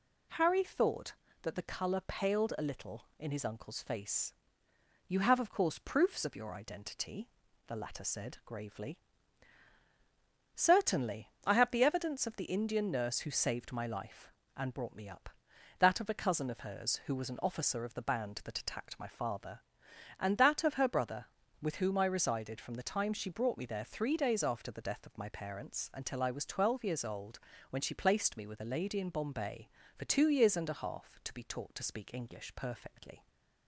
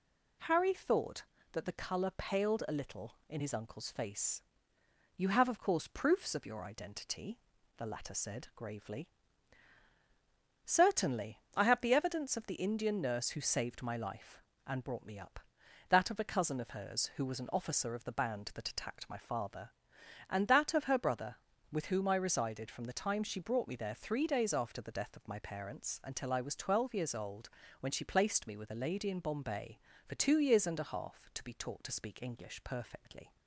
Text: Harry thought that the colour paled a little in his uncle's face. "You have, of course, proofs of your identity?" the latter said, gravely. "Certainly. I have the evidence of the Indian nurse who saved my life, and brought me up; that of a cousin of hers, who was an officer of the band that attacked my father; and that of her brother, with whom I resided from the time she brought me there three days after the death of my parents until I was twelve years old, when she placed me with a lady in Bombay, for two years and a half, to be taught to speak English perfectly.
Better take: neither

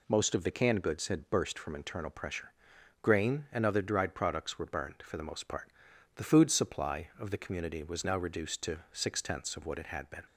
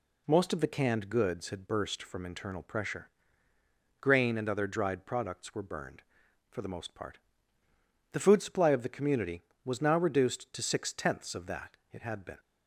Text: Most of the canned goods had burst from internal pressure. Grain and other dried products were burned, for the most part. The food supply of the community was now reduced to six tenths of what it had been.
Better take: first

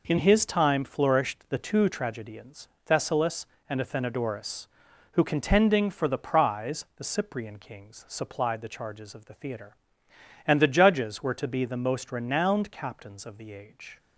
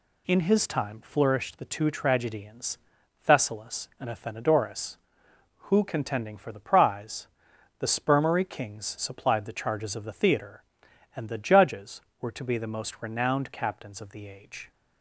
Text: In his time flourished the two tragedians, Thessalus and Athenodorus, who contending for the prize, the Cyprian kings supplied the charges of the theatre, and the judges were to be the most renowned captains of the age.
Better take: first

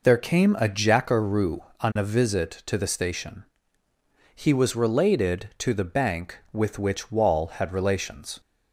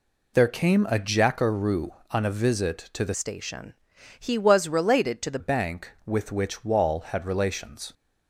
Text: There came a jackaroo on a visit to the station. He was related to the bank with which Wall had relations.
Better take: first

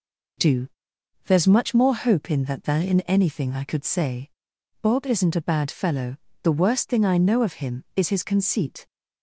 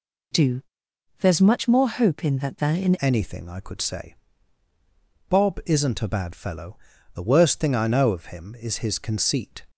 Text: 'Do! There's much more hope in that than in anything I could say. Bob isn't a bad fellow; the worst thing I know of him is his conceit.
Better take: first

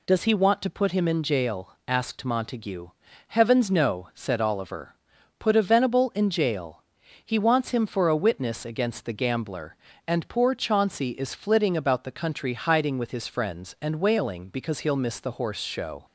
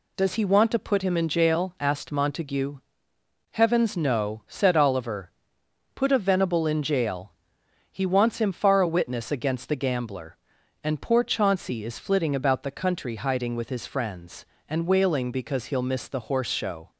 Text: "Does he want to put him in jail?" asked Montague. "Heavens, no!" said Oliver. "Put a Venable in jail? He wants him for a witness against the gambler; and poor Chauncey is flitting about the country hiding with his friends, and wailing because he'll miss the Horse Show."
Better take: first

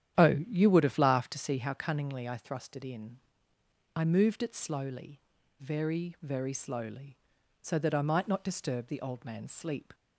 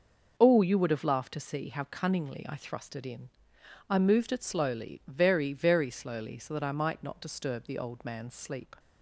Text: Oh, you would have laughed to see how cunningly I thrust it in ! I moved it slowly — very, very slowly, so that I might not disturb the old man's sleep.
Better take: second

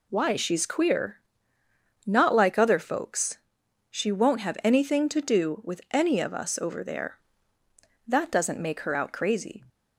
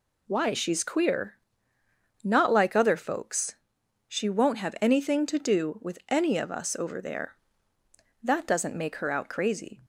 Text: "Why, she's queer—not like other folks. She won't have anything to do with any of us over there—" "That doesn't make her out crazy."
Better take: neither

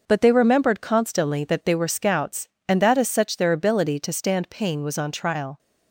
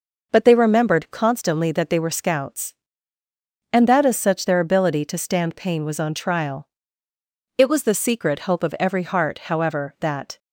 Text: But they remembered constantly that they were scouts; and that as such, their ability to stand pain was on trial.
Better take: first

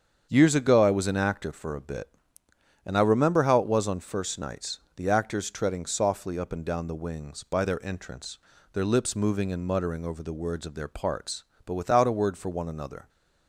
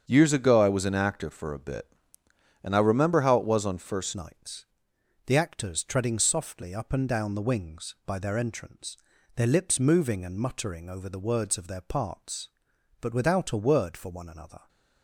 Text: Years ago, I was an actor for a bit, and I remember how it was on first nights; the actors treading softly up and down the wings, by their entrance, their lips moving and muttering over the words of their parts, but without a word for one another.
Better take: first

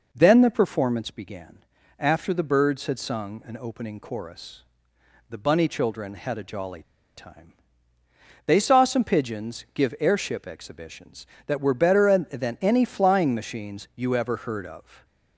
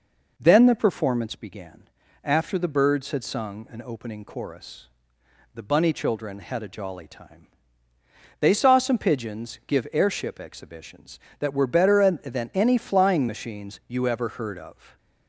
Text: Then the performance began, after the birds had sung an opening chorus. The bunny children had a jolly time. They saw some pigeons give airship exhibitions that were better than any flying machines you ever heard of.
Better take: second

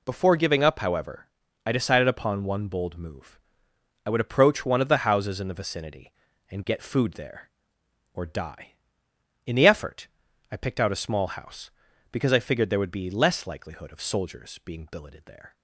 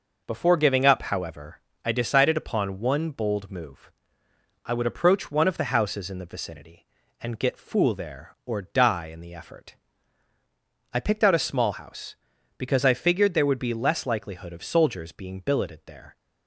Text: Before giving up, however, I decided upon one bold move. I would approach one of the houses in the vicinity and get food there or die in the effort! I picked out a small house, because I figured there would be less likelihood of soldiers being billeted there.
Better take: first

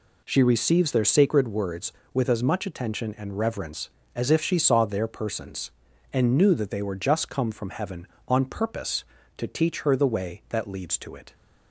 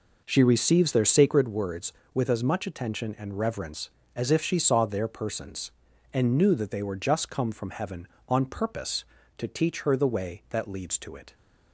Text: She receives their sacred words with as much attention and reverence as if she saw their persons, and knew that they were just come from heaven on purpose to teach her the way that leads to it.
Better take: first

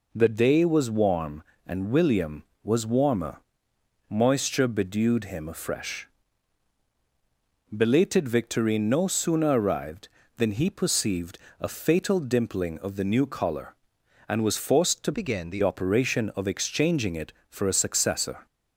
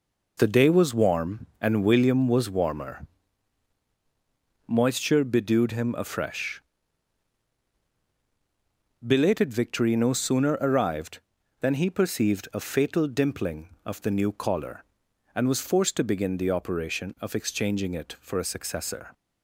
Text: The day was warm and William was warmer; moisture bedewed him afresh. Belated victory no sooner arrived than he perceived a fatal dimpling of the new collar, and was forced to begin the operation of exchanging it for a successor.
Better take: second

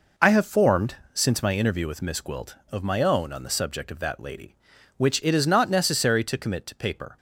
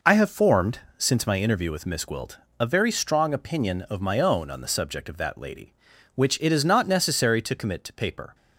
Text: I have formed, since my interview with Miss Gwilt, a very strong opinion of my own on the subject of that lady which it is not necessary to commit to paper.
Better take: second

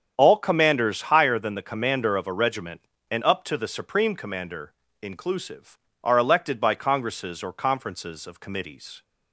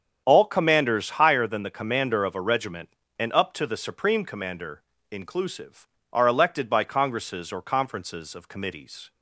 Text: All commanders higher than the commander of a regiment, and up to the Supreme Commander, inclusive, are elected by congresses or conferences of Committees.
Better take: neither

